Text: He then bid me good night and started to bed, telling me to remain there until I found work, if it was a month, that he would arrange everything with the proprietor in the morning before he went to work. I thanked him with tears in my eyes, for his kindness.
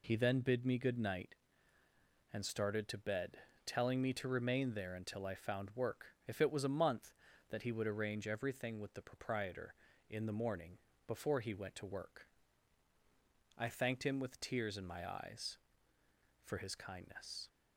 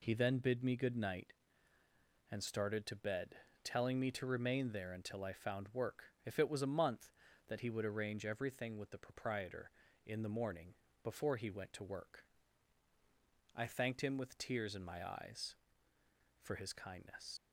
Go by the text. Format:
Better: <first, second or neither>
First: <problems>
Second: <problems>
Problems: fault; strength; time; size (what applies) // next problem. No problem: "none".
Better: first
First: pauses between "morning" and "before"; slight; at 10.7 s; 0.30 s long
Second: pauses between "morning" and "before"; slight; at 10.7 s; 0.30 s long // leaves "kindness" unfinished; at 17.3 s; 80 ms